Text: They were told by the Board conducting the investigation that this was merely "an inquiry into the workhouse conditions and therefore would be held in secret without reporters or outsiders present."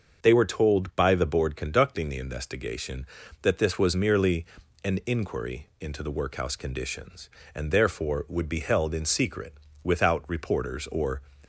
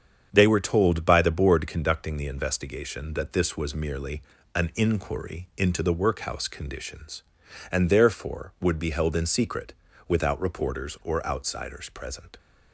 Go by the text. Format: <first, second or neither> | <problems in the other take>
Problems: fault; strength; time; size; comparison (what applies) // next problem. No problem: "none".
second | starts louder than the rest; until 1.2 s; 6.5 dB; strong in the second // pauses between "merely" and "an"; slight; at 4.4 s; 0.36 s long; slight in the second // pauses between "secret" and "without"; slight; at 9.5 s; 0.30 s long; slight in the second // stops before "outsiders present"; at 11.4 s